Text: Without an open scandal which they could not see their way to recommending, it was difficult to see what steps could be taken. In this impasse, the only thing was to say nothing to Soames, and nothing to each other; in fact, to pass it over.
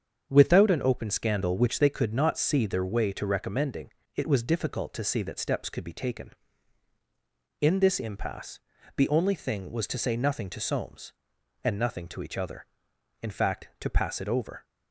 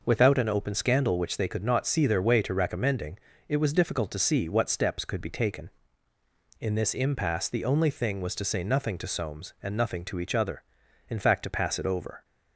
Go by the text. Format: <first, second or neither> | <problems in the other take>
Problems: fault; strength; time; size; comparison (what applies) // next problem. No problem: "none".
second | starts louder than the rest; strong; until 1.3 s; 7.5 dB // says "that" for "what"; at 5.2 s